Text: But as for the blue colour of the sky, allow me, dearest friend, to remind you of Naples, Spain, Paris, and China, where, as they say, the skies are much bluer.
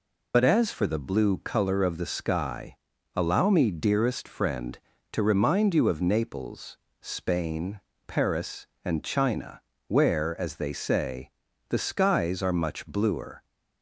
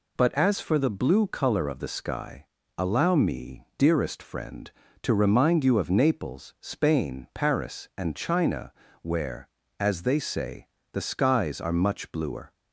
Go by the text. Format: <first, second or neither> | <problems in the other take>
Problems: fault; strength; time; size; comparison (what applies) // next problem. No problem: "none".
second | loses the start of "But"; at 0.3 s; 45 ms